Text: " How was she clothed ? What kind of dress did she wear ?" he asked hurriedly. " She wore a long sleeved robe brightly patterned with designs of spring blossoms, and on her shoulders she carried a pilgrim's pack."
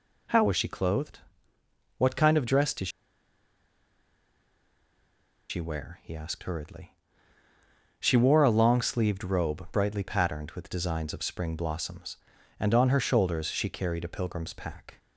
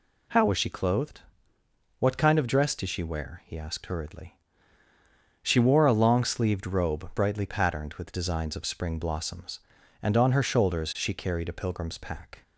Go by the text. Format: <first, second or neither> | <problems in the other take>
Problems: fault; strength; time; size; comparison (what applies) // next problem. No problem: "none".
second | pauses between "did" and "she"; strong; at 2.8 s; 2.6 s long